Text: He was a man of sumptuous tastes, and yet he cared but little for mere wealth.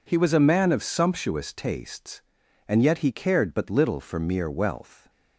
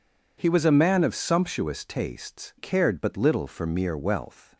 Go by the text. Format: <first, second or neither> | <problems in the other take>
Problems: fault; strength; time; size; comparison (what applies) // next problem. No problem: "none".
first | skips "and yet he"; at 2.5 s